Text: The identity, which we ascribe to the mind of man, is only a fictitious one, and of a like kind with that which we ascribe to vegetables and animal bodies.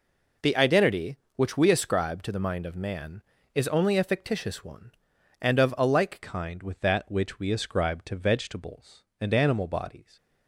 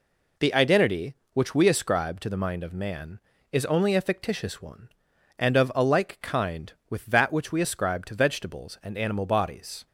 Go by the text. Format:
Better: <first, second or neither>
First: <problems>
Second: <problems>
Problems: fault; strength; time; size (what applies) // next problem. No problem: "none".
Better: second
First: changes voice at "kind"; from 6.2 s on; 3.9 s long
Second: none